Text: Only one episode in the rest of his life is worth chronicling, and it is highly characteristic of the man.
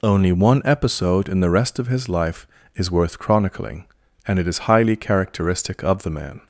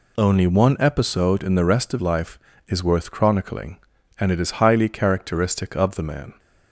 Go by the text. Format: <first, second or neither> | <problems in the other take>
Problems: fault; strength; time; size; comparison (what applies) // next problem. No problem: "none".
first | skips "his"; at 1.9 s